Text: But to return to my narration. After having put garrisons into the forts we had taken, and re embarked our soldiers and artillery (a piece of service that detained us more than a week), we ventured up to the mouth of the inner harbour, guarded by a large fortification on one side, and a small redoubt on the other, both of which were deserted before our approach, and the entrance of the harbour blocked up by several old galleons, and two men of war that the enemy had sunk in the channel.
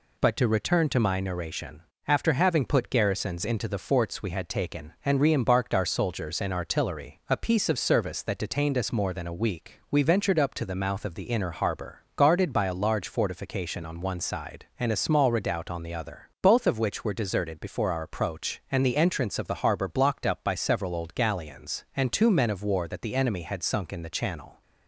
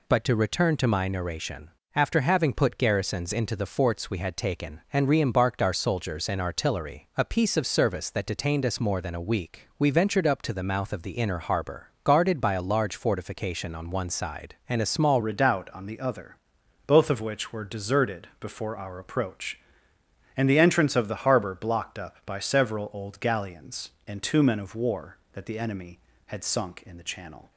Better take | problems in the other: first | changes voice at "redoubt"; from 15.2 s on; 12.3 s long

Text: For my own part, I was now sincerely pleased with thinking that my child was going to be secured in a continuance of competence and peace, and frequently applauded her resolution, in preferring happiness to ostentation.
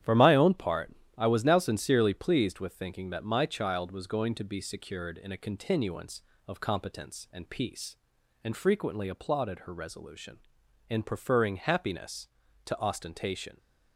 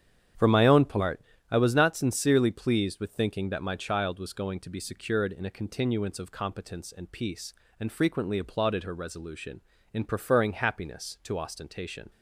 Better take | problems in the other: first | starts louder than the rest; strong; until 1.6 s; 9 dB; strong in the first // says "not" for "now"; at 1.7 s

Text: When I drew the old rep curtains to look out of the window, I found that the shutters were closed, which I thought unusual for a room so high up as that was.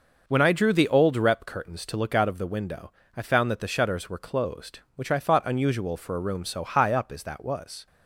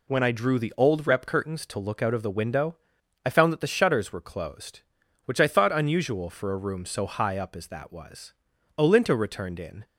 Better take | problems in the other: first | goes on to say "Olinto returned in"; noticeable; from 8.7 s on; 1.0 s long

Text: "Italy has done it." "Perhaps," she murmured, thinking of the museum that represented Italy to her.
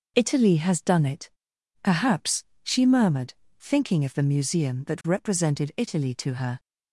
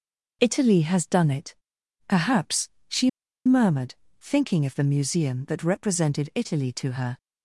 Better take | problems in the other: first | pauses between "she" and "murmured"; at 3.0 s; 0.36 s long

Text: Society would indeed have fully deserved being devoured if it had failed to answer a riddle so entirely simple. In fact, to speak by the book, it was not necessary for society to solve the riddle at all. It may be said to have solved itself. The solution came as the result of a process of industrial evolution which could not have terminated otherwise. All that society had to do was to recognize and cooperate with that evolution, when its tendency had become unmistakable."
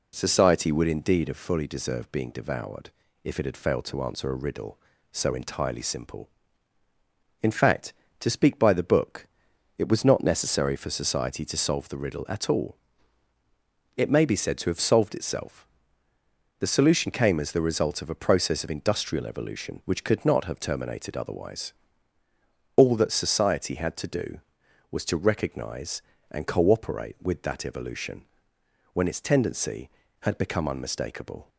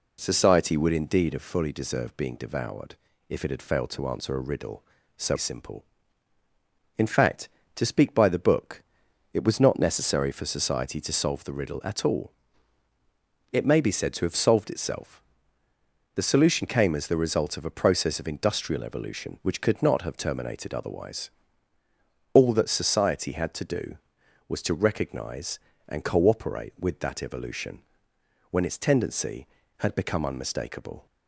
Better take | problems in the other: first | pauses between "devoured" and "if"; slight; at 2.9 s; 0.34 s long; slight in the first // skips "entirely"; at 5.3 s

